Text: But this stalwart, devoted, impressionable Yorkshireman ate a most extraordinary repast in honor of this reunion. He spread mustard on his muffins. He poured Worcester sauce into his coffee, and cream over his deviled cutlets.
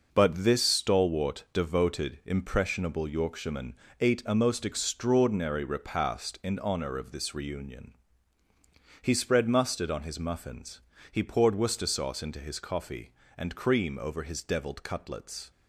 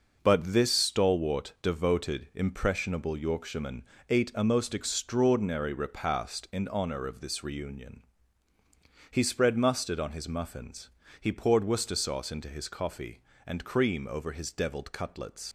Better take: first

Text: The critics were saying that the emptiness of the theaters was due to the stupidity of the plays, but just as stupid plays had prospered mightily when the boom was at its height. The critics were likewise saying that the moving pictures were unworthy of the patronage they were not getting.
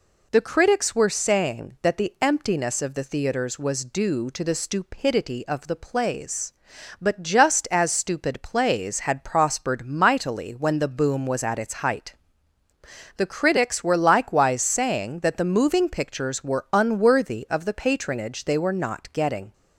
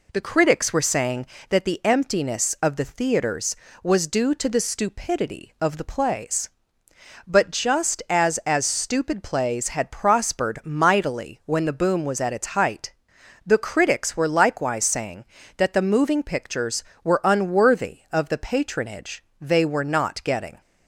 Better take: first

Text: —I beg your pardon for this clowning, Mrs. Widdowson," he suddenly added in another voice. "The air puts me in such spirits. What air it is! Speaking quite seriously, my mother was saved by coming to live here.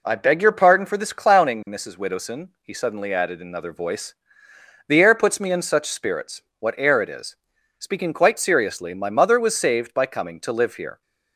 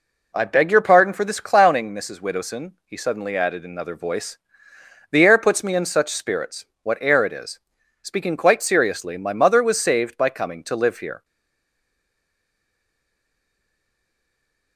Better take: first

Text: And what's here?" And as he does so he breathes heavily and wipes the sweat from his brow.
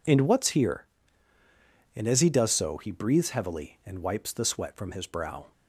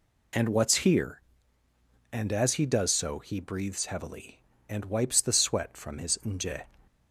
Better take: first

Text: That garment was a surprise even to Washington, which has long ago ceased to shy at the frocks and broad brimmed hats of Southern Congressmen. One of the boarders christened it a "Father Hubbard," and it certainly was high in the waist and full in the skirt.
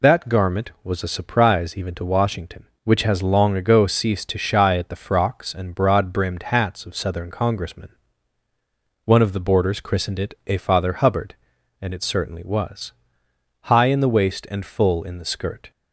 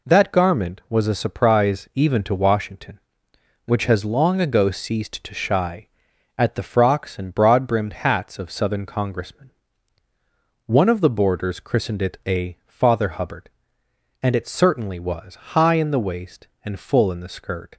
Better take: second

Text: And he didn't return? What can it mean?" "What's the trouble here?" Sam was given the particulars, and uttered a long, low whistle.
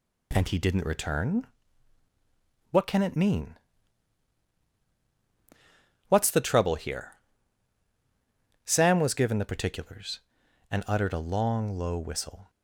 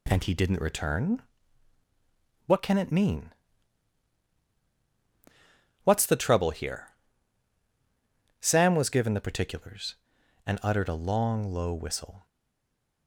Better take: first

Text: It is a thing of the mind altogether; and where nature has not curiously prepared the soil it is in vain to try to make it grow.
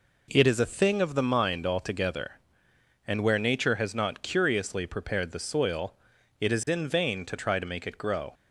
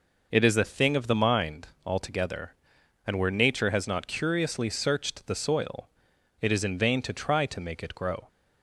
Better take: first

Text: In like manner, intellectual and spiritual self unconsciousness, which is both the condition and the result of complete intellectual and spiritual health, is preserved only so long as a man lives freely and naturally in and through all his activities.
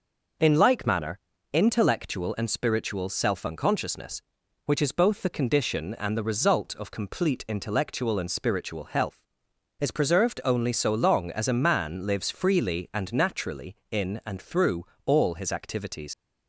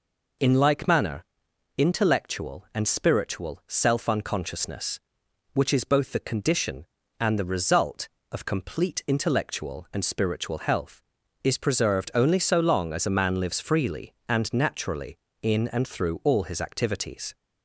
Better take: second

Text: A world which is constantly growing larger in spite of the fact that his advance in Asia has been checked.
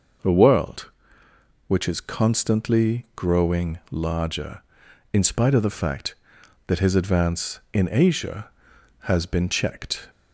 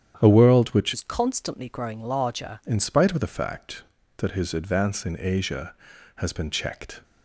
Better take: first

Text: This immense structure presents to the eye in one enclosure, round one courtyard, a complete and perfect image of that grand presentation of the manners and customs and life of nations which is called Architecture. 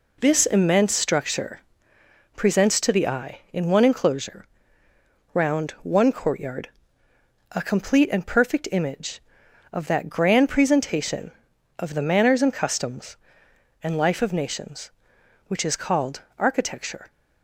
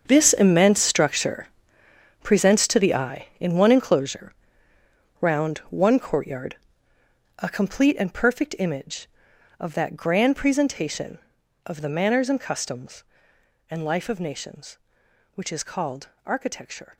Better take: first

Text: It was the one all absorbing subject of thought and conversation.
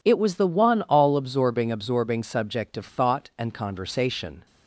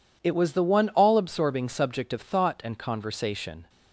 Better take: second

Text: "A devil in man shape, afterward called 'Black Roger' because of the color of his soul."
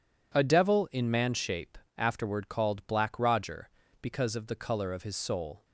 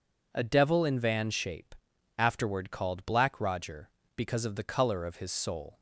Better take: first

